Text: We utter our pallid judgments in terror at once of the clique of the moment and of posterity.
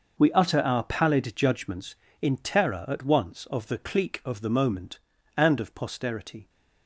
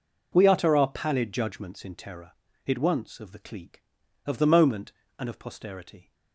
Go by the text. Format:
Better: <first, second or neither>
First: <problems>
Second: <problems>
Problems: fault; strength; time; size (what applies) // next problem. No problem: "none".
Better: first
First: none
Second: says "it" for "at"; at 2.6 s